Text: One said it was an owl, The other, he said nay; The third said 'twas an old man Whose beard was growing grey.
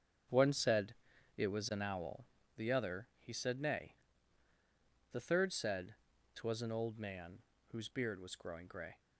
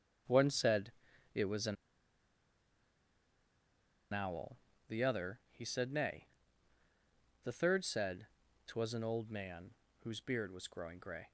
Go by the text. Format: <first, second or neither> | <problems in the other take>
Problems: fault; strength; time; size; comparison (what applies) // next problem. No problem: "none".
first | starts louder than the rest; until 1.7 s; 7 dB; also in the first // pauses between "said" and "it"; at 0.9 s; 0.44 s long; also in the first // pauses between "an" and "owl"; strong; at 1.7 s; 2.3 s long // pauses between "said" and "twas"; at 8.2 s; 0.40 s long; also in the first // pauses between "man" and "Whose"; slight; at 9.7 s; 0.30 s long; slight in the first